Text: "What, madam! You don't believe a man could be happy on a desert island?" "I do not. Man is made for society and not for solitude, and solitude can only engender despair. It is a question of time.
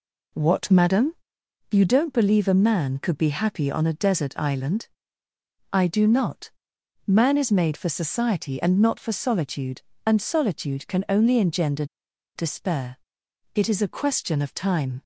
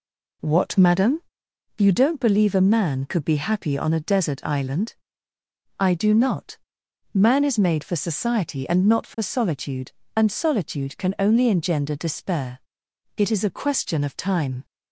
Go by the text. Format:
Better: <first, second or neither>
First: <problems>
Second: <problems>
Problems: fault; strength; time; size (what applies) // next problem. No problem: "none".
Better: second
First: pauses between "engender" and "despair"; noticeable; at 11.8 s; 0.50 s long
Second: none